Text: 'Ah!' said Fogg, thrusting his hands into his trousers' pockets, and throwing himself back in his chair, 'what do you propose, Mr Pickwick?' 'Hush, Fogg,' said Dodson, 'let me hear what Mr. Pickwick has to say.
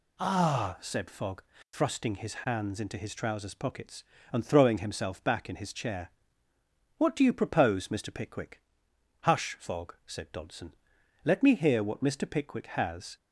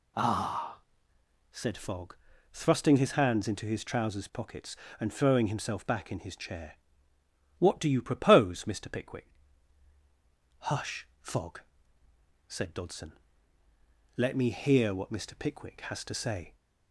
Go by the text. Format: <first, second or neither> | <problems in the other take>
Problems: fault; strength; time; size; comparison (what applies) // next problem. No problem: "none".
second | stops before "to say"; at 13.1 s